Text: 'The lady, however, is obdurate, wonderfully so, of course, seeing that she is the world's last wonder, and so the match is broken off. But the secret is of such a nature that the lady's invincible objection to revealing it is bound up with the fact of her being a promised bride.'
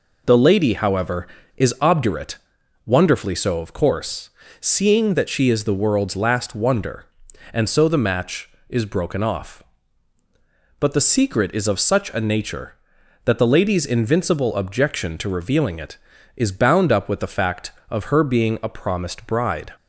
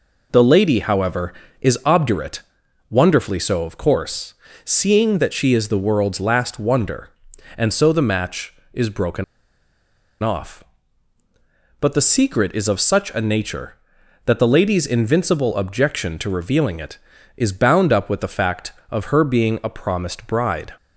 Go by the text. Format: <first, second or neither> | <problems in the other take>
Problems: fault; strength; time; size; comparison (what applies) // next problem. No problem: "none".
first | pauses between "broken" and "off"; at 9.2 s; 0.99 s long